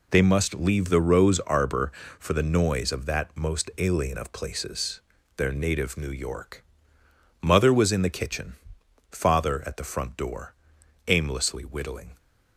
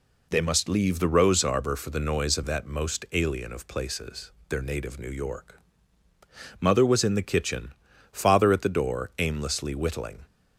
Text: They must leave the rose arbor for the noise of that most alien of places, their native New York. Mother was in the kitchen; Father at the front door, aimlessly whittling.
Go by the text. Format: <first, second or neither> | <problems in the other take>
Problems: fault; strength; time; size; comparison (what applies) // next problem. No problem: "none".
first | skips "front"; at 8.6 s